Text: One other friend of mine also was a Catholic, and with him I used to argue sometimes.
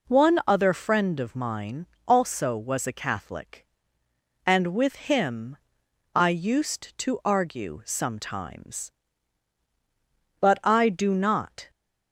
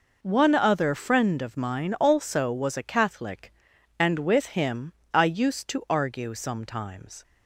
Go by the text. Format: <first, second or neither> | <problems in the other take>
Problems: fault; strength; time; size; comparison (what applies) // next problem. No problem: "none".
second | pauses between "mine" and "also"; slight; at 1.8 s; 0.18 s long // pauses between "with" and "him"; slight; at 4.9 s; 0.16 s long // pauses between "him" and "I"; noticeable; at 5.5 s; 0.58 s long; slight in the second // goes on to say "But I do not"; noticeable; from 10.3 s on; 1.3 s long